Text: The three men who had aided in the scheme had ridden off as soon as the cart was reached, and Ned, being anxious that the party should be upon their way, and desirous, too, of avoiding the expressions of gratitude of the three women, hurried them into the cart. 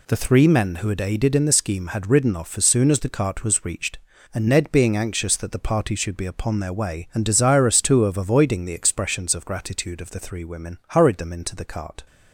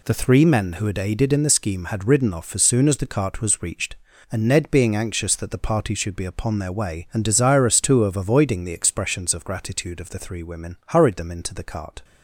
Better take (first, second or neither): neither